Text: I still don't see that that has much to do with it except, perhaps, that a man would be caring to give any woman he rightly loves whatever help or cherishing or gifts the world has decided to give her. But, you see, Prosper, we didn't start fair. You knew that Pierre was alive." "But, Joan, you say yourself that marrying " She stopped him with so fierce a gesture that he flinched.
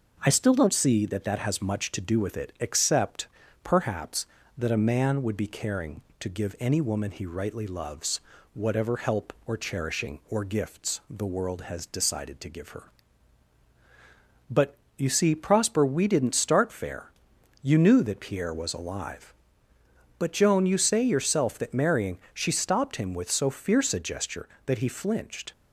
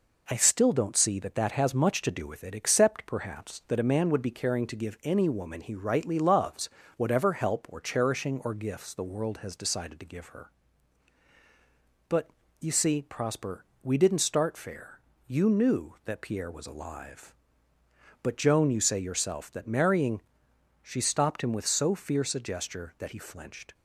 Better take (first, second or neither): neither